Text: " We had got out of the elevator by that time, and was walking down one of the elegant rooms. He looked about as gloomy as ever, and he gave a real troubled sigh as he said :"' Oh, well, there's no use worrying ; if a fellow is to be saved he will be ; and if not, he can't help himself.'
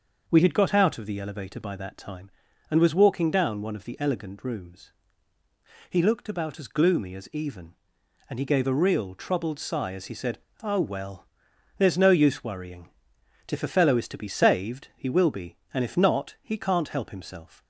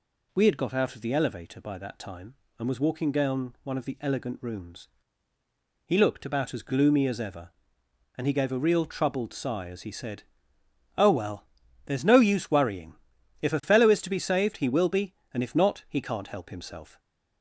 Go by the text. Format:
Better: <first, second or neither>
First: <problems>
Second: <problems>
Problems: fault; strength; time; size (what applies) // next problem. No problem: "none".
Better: second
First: starts louder than the rest; until 1.2 s; 6.5 dB // says "even" for "ever"; at 7.3 s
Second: none